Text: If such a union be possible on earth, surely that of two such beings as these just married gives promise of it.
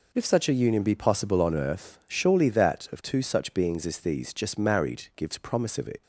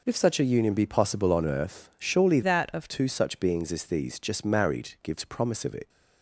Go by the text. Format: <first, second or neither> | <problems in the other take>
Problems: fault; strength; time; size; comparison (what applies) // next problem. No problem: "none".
first | changes voice from "that" to "of"; from 2.4 to 2.8 s; 0.4 s long